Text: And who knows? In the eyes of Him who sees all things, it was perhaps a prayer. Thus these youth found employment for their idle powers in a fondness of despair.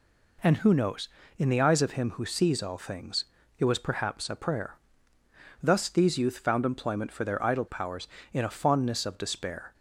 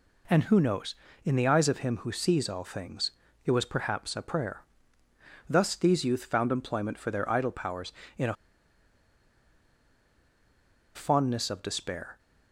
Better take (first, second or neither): first